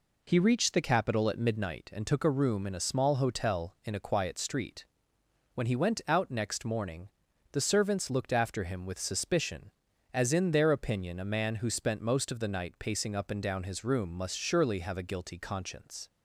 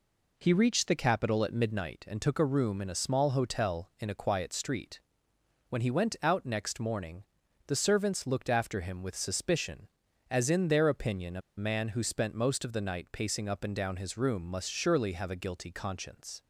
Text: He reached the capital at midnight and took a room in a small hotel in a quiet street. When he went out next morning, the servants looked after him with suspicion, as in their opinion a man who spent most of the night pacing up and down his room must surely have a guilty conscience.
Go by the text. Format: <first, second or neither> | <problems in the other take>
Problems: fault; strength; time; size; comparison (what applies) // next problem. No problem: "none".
first | pauses between "a" and "man"; slight; at 11.4 s; 0.16 s long